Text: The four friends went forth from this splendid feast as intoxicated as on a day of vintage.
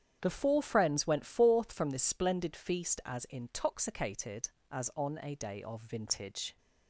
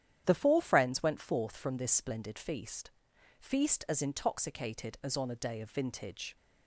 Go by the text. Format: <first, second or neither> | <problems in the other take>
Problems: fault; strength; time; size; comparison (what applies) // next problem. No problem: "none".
first | starts louder than the rest; strong; until 1.2 s; 10 dB; strong in the first // says "feast" twice; at 3.3 s